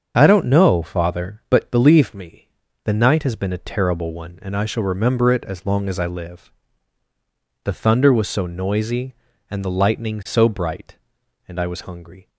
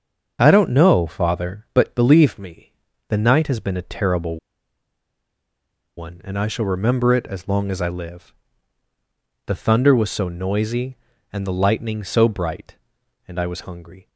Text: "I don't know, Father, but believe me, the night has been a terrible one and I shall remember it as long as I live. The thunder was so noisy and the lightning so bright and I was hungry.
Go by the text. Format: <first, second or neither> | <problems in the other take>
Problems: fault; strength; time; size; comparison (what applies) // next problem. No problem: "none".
first | starts louder than the rest; until 1.4 s; 7 dB; also in the first // pauses between "terrible" and "one"; strong; at 4.3 s; 1.5 s long